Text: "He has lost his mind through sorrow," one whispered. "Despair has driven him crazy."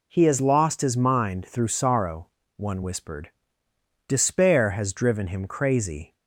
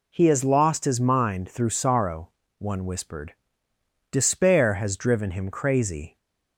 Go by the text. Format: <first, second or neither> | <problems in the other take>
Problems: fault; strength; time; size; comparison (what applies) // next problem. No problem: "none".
neither | none